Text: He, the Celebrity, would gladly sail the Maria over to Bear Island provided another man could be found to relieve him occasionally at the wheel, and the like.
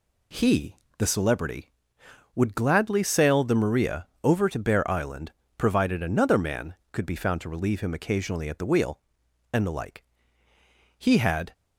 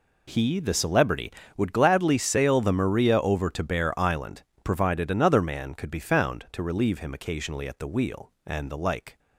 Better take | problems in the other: second | pauses between "Maria" and "over"; slight; at 4.0 s; 0.16 s long // pauses between "Island" and "provided"; slight; at 5.3 s; 0.26 s long; slight in the second // goes on to say "He had"; from 10.9 s on; 0.54 s long

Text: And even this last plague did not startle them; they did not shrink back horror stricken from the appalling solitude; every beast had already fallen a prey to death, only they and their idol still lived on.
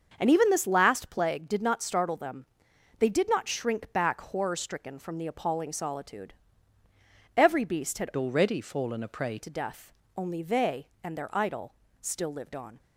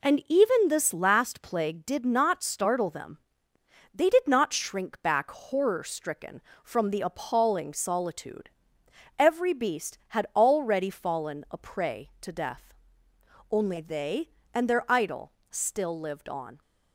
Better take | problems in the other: second | starts louder than the rest; until 1.1 s; 6.5 dB // changes voice from "already" to "prey"; from 8.1 to 9.3 s; 1.2 s long // pauses between "idol" and "still"; slight; at 11.7 s; 0.26 s long; slight in the second

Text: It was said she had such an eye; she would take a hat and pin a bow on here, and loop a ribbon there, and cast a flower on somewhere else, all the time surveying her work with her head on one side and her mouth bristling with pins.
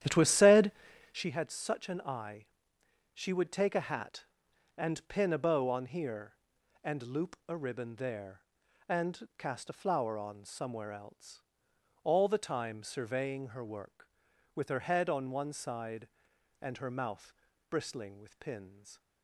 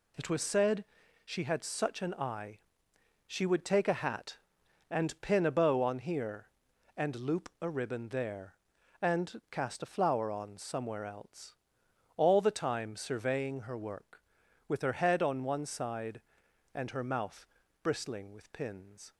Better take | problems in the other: second | starts louder than the rest; strong; until 1.3 s; 11 dB // pauses between "said" and "she"; at 0.7 s; 0.40 s long; also in the second // pauses between "mouth" and "bristling"; at 17.3 s; 0.38 s long; also in the second

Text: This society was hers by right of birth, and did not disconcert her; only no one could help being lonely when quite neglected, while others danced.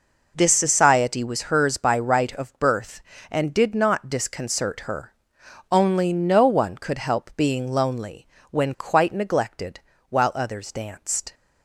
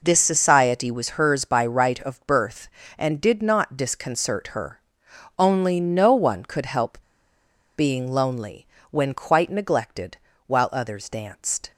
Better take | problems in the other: first | pauses between "help" and "being"; noticeable; at 6.9 s; 0.78 s long // pauses between "lonely" and "when"; slight; at 8.6 s; 0.24 s long; slight in the first

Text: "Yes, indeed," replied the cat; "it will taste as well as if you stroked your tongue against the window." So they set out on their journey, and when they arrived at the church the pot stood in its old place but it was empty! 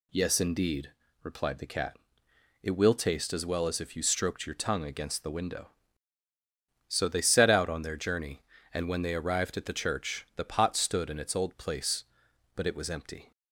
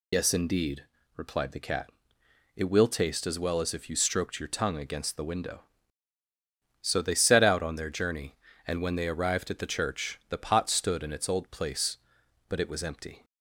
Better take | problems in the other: first | loses the start of "Yes"; at 0.1 s; 85 ms

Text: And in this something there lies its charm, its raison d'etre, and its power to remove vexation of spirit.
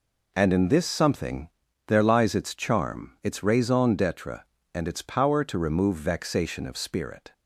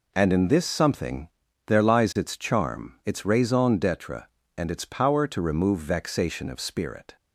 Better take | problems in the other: neither | pauses between "something" and "there"; the same in both

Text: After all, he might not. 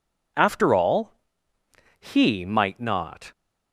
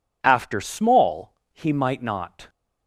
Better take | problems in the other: first | says "small" for "all"; at 0.5 s

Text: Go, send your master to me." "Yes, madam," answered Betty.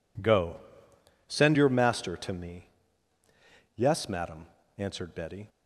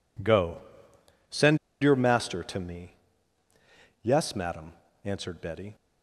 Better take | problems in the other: first | pauses between "send" and "your"; slight; at 1.5 s; 0.25 s long

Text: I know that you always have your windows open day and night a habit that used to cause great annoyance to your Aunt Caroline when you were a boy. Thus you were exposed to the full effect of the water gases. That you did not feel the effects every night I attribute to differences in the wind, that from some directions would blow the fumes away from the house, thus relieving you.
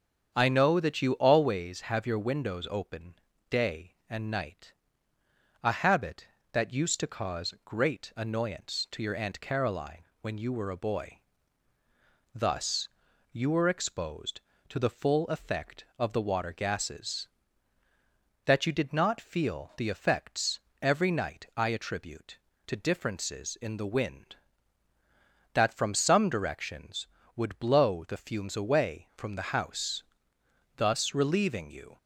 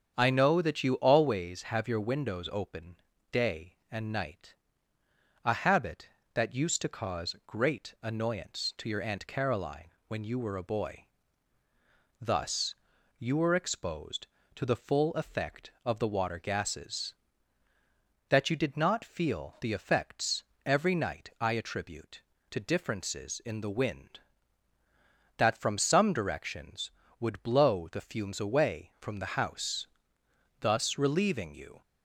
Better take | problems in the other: neither | starts louder than the rest; strong; the same in both // pauses between "open" and "day"; slight; the same in both // pauses between "night" and "a"; noticeable; the same in both // pauses between "Caroline" and "when"; slight; the same in both // pauses between "Thus" and "you"; the same in both // pauses between "effects" and "every"; slight; the same in both

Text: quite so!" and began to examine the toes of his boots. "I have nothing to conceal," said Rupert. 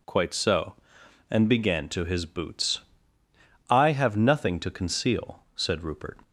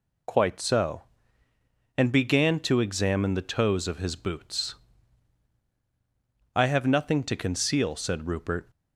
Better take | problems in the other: second | skips "examine the toes of"; at 2.0 s

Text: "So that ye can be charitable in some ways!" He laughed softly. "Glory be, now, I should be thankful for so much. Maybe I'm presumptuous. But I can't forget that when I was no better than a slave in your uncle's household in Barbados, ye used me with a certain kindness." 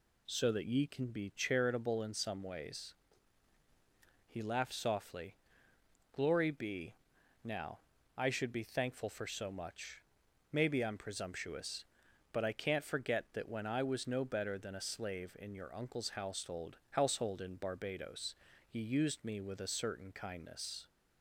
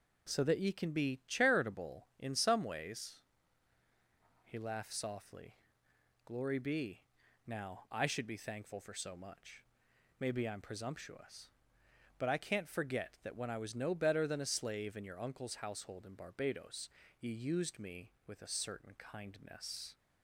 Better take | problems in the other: second | says "household" twice; at 16.8 s

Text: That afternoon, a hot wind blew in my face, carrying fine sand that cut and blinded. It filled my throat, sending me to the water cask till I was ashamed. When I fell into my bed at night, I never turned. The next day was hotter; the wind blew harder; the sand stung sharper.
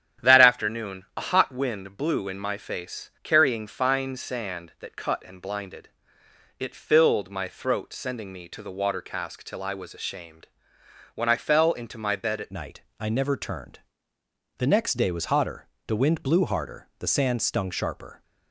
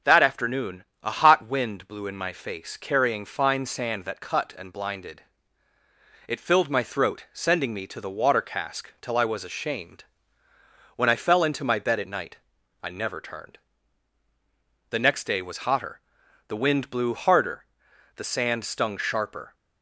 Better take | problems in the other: second | starts louder than the rest; strong; until 1.3 s; 9.5 dB // changes voice at "night"; from 12.5 s on; 5.7 s long

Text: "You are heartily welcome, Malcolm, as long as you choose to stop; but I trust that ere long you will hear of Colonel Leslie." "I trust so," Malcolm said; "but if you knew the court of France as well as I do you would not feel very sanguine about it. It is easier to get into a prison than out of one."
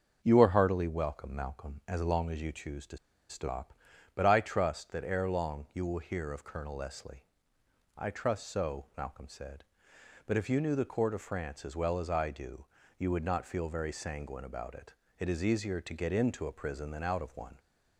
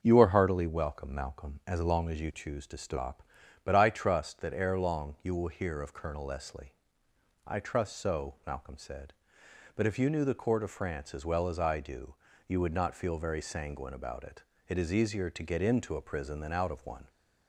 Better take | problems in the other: second | starts louder than the rest; until 1.2 s; 6.5 dB; also in the second // pauses between "to" and "stop"; slight; at 2.9 s; 0.33 s long // pauses between "do" and "you"; slight; at 12.6 s; 0.32 s long; slight in the second

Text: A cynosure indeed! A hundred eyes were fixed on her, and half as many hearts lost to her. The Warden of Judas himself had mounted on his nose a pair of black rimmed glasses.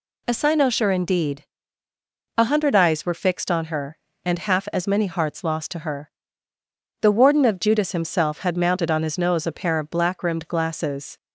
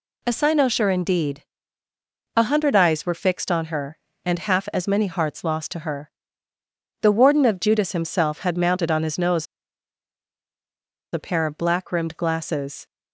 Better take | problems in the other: first | pauses between "nose" and "a"; strong; at 9.4 s; 1.6 s long

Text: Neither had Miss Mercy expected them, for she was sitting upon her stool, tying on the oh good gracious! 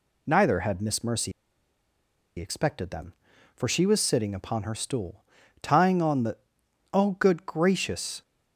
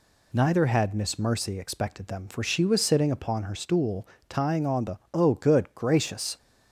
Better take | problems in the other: second | pauses between "Mercy" and "expected"; at 1.3 s; 1.0 s long // pauses between "the" and "oh"; noticeable; at 6.3 s; 0.56 s long; slight in the second

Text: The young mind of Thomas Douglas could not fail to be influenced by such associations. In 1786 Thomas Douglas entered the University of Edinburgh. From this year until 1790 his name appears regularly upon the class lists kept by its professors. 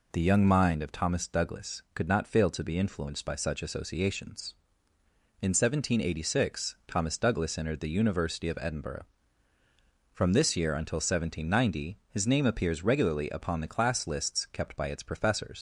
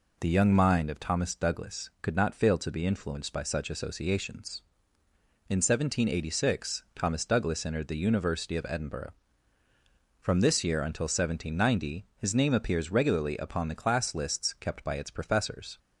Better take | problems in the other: second | leaves "professors" unfinished; at 15.5 s; 95 ms

